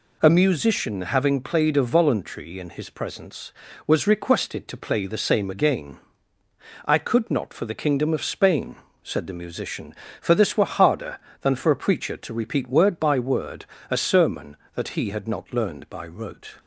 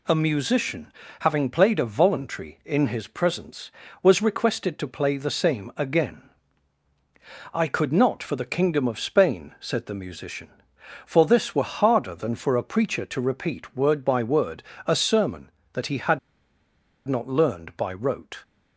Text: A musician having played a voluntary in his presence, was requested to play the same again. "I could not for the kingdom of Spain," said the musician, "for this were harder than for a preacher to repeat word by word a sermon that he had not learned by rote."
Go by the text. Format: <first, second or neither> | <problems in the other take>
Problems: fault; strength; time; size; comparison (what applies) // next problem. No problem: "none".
first | pauses between "musician" and "having"; slight; at 0.9 s; 0.28 s long // pauses between "word" and "a"; slight; at 14.6 s; 0.24 s long; slight in the first // pauses between "had" and "not"; noticeable; at 16.1 s; 0.89 s long